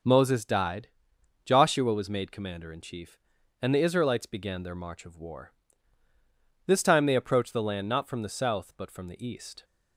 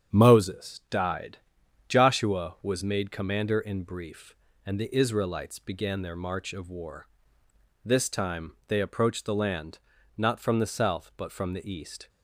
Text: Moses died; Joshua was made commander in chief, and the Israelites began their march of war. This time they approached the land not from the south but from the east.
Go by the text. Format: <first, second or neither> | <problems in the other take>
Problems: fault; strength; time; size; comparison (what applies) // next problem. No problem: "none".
first | starts louder than the rest; strong; until 1.2 s; 8 dB // says "brief" for "chief"; at 3.8 s // pauses between "land" and "not"; at 9.7 s; 0.38 s long